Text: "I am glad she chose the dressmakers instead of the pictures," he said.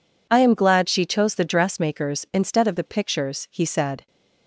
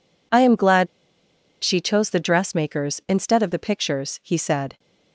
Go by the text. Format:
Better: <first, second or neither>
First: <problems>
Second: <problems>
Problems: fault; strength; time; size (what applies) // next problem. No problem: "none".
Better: first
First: none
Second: pauses between "glad" and "she"; noticeable; at 0.8 s; 0.75 s long